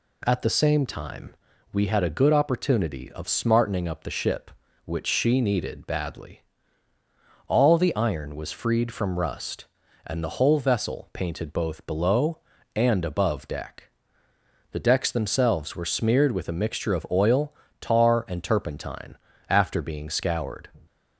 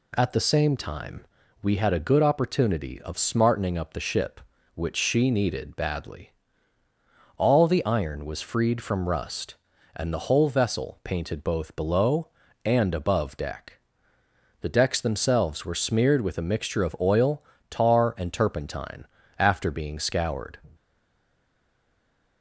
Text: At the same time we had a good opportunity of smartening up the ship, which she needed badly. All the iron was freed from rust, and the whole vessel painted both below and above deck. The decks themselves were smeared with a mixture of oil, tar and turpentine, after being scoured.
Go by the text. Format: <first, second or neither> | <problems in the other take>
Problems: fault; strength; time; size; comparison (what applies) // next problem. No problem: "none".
first | pauses between "time" and "we"; at 1.2 s; 0.37 s long; also in the first // stays silent after the last word; noticeable; from 20.7 s on; 1.7 s long